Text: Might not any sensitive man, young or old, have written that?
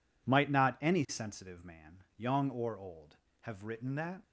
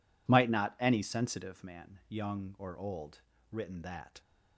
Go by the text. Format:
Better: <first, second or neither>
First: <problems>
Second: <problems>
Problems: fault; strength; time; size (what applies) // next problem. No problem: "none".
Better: first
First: none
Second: skips "have"; at 3.3 s